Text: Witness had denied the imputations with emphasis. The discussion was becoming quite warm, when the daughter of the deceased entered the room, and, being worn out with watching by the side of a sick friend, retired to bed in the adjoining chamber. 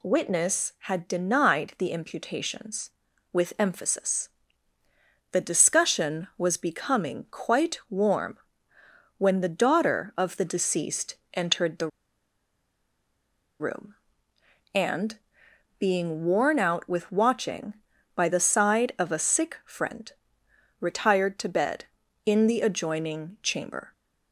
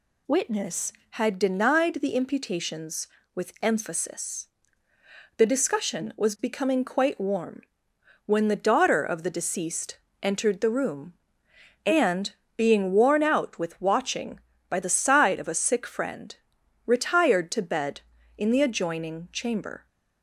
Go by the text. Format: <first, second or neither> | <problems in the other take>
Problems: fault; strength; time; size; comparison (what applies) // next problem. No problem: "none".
second | pauses between "deceased" and "entered"; slight; at 11.1 s; 0.16 s long; slight in the second // pauses between "the" and "room"; strong; at 11.8 s; 1.7 s long